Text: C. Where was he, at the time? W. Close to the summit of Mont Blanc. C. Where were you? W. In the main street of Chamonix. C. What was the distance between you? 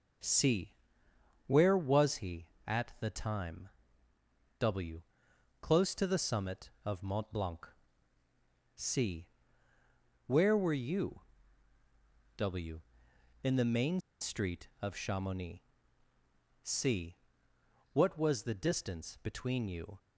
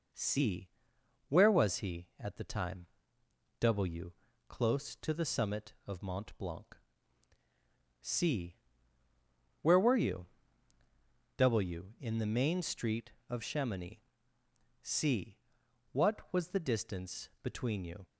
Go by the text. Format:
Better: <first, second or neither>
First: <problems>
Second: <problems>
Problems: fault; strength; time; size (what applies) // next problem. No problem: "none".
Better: second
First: pauses between "main" and "street"; slight; at 14.0 s; 0.20 s long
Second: none